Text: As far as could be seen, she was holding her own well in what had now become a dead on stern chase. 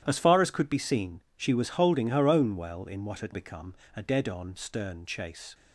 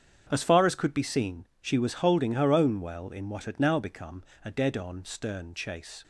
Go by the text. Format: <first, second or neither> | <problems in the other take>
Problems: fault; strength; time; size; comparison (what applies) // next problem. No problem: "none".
second | starts louder than the rest; strong; until 1.0 s; 11 dB; strong in the second // skips "now"; at 3.3 s // pauses between "become" and "a"; slight; at 3.7 s; 0.20 s long; slight in the second